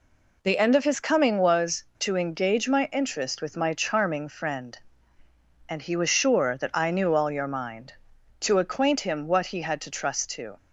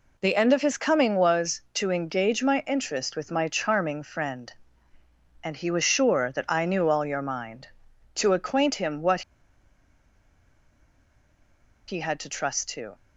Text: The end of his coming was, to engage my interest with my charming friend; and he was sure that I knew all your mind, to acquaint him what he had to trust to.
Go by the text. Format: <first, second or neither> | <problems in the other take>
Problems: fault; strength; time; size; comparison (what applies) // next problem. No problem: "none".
first | pauses between "what" and "he"; strong; at 9.2 s; 2.6 s long